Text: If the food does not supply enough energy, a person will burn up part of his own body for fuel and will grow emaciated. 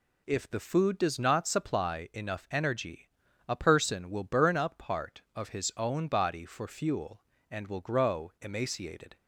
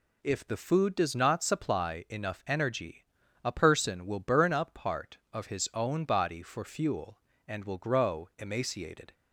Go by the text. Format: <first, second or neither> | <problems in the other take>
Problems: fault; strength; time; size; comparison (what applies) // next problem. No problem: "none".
neither | none